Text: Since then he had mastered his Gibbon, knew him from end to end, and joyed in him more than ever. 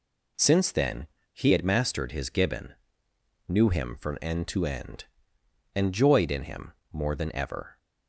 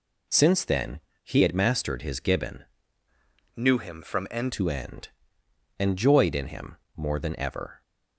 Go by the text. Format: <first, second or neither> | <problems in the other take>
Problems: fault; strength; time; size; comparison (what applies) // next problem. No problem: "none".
first | pauses between "then" and "he"; slight; at 0.9 s; 0.24 s long; slight in the first // changes voice from "knew" to "end"; from 3.5 to 4.5 s; 1.0 s long // pauses between "him" and "more"; slight; at 6.7 s; 0.20 s long; slight in the first